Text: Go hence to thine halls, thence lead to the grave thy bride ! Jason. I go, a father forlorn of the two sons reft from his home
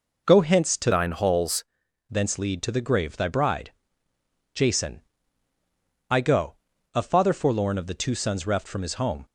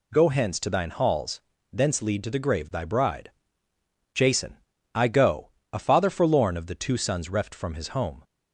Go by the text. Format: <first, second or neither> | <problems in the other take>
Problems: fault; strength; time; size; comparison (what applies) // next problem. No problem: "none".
second | changes voice from "thine" to "halls"; from 0.9 to 1.6 s; 0.7 s long